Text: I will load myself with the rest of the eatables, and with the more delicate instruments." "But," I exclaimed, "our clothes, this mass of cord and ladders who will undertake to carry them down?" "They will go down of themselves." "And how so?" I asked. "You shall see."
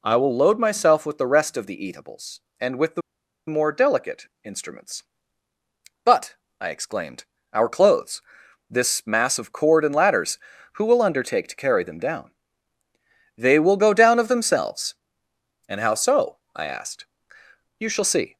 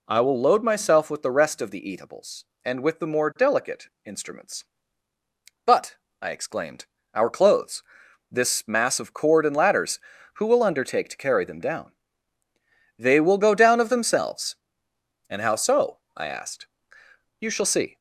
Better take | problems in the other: second | pauses between "the" and "more"; noticeable; at 3.0 s; 0.48 s long // pauses between "delicate" and "instruments"; slight; at 4.2 s; 0.18 s long; slight in the second

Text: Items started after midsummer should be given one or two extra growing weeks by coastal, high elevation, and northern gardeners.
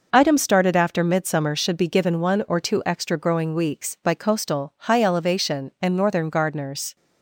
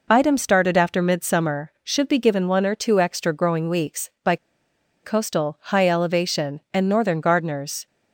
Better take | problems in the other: first | pauses between "by" and "coastal"; noticeable; at 4.3 s; 0.67 s long

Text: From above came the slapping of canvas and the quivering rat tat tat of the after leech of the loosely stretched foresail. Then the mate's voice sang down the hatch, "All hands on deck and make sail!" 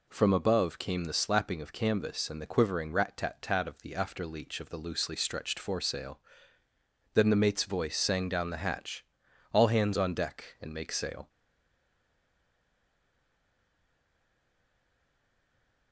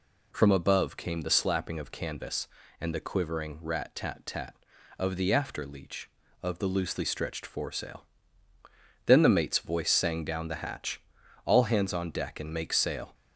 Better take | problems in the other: second | stays silent after the last word; strong; from 11.2 s on; 4.7 s long

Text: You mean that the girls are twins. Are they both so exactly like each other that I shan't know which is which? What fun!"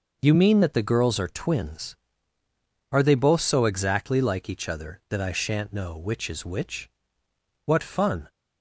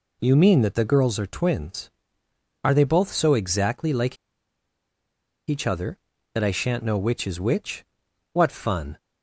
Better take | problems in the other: first | pauses between "like" and "each"; strong; at 4.1 s; 1.3 s long

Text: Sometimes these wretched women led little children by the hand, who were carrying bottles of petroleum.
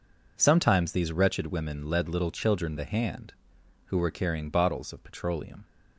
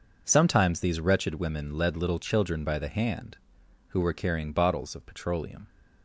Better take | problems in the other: second | skips "by"; at 2.7 s

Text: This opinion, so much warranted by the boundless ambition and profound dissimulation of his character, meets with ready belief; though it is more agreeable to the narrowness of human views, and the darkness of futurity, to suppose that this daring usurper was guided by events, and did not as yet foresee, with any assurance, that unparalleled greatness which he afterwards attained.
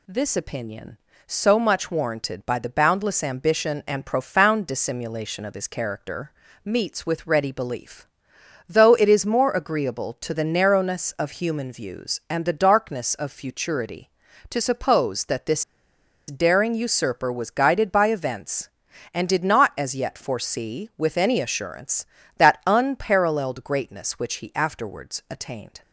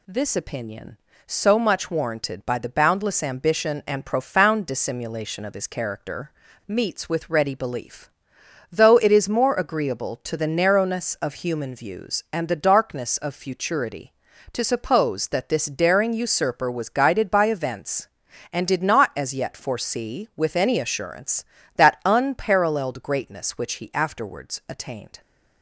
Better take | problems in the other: second | pauses between "this" and "daring"; noticeable; at 15.6 s; 0.66 s long

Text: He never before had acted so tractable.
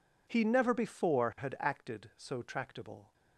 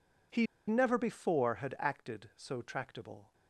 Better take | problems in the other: first | pauses between "He" and "never"; slight; at 0.4 s; 0.22 s long

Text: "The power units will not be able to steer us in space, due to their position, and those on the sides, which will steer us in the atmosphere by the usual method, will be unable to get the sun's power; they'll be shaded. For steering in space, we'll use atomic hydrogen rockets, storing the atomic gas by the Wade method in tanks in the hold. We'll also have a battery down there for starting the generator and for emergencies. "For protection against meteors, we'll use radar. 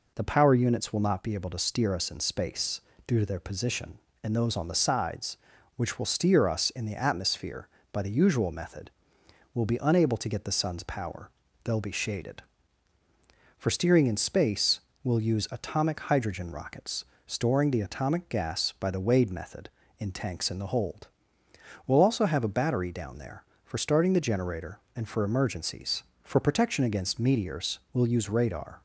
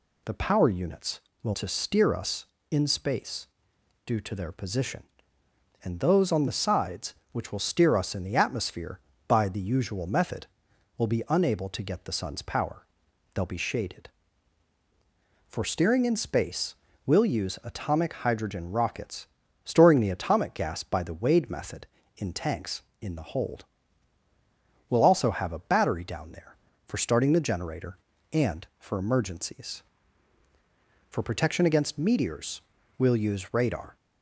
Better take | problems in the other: first | skips "not be able"; at 1.5 s

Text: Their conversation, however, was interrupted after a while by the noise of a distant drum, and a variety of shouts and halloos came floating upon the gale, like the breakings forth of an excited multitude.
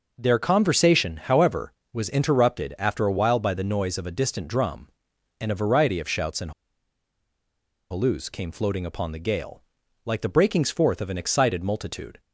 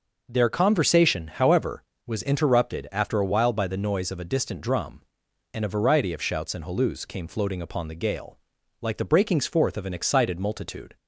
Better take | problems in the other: second | pauses between "and" and "halloos"; strong; at 6.5 s; 1.4 s long

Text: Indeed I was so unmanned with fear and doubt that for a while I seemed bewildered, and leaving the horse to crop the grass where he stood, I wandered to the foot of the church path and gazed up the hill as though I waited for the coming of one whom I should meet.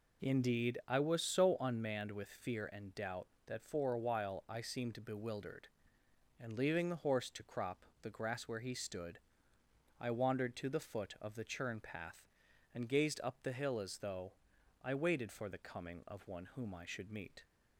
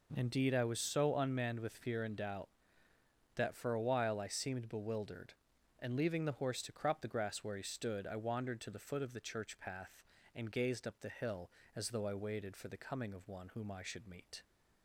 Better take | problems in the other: second | pauses between "crop" and "the"; slight; at 7.8 s; 0.16 s long // says "churn" for "church"; at 11.4 s // pauses between "though" and "I"; noticeable; at 14.3 s; 0.52 s long

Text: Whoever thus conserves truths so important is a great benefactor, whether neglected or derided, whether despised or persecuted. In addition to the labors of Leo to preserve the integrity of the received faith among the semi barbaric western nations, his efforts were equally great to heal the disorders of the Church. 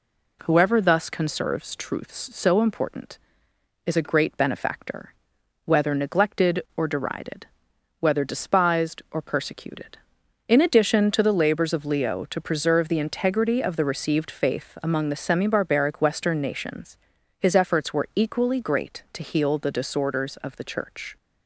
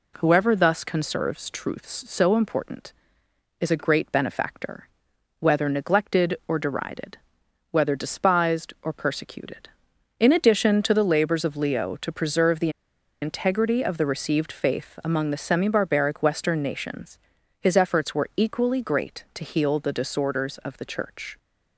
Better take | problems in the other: first | pauses between "the" and "integrity"; noticeable; at 12.6 s; 0.52 s long

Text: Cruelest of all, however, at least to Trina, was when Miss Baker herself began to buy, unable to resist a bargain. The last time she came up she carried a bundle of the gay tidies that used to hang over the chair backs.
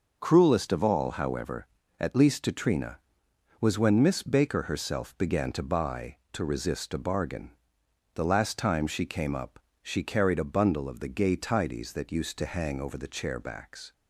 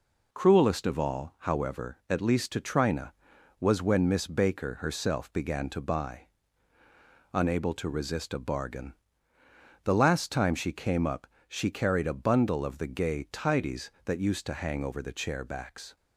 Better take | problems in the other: second | skips "unable"; at 6.2 s // pauses between "up" and "she"; slight; at 9.5 s; 0.24 s long; slight in the second

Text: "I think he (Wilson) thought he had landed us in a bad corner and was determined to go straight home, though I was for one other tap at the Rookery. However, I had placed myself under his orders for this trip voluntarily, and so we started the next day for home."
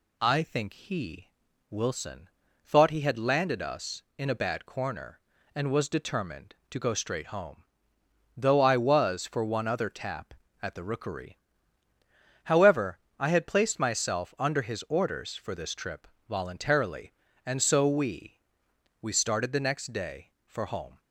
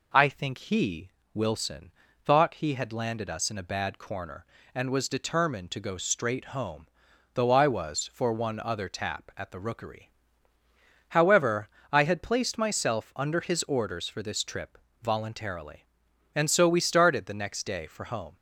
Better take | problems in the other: second | pauses between "trip" and "voluntarily"; slight; at 16.0 s; 0.22 s long; slight in the second // says "we" twice; at 19.0 s

